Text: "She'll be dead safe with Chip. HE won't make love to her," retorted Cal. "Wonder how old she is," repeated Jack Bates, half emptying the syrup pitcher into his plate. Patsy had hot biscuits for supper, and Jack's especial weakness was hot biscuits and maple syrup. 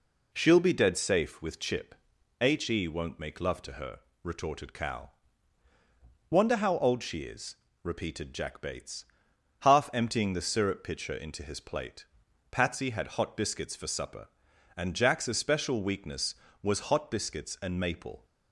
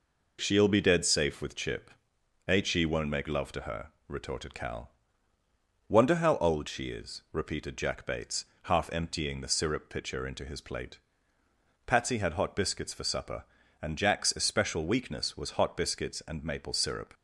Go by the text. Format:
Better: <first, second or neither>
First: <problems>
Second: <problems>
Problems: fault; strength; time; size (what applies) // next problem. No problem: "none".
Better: second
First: stops before "syrup"; at 18.2 s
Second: none